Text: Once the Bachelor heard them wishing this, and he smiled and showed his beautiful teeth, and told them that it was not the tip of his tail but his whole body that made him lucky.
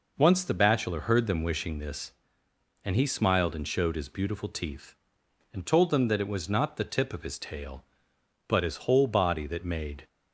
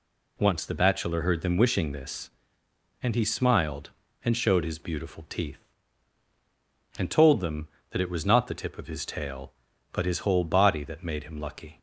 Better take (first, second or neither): second